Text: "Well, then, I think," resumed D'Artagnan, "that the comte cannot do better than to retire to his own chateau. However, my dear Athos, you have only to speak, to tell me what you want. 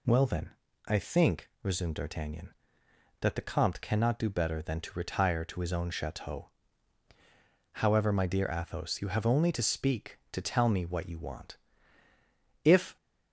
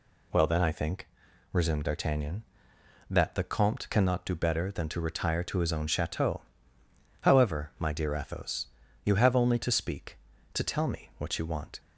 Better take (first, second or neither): second